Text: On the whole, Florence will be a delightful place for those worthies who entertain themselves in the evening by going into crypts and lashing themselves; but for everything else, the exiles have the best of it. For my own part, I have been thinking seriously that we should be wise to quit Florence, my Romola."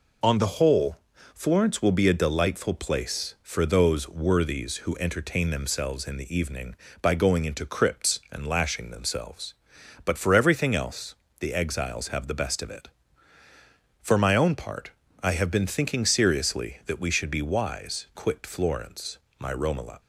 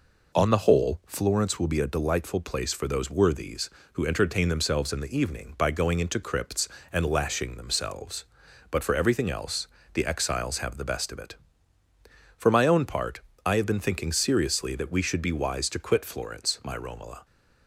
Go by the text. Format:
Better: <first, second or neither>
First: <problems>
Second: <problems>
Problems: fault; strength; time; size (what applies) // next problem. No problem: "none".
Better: second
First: skips "to"; at 18.1 s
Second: none